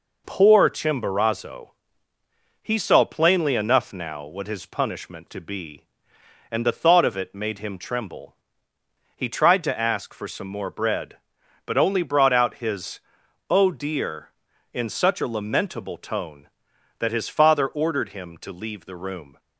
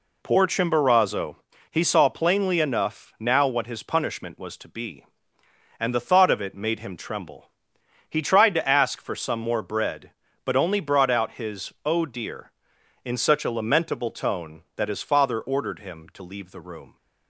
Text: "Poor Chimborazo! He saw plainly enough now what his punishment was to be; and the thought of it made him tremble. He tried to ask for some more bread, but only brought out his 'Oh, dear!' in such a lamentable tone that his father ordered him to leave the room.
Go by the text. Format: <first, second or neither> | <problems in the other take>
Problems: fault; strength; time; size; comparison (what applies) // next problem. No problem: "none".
second | skips "was"; at 5.2 s // pauses between "his" and "Oh"; noticeable; at 12.9 s; 0.50 s long